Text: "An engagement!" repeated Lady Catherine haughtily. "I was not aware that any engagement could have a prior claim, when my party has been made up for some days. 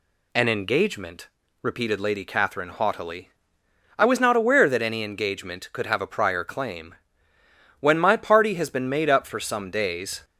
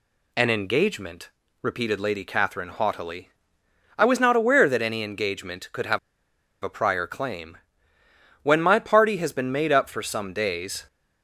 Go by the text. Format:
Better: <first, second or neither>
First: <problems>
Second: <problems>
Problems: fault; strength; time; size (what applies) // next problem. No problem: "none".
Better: first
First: none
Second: pauses between "have" and "a"; noticeable; at 5.9 s; 0.63 s long